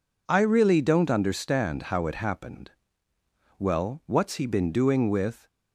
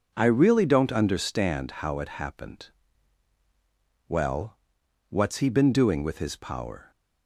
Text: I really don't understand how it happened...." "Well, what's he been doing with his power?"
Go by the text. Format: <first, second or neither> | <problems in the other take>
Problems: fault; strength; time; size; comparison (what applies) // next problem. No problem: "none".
second | stops before "his power"; at 5.4 s